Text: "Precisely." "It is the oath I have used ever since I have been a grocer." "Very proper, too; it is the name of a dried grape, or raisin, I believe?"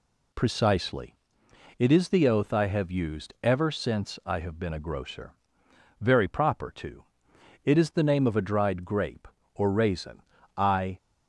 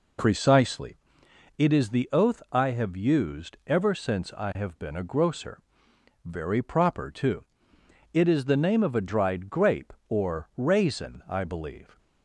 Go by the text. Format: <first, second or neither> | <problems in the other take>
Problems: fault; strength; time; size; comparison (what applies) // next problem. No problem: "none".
second | stops before "believe"; at 10.9 s